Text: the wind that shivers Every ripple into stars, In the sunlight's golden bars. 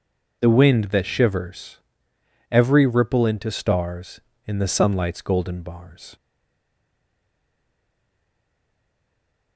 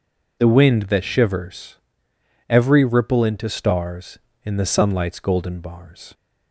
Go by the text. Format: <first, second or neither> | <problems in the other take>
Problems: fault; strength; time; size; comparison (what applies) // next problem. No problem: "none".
second | pauses between "shivers" and "Every"; noticeable; at 1.7 s; 0.72 s long; noticeable in the second // stays silent after the last word; strong; from 6.1 s on; 3.4 s long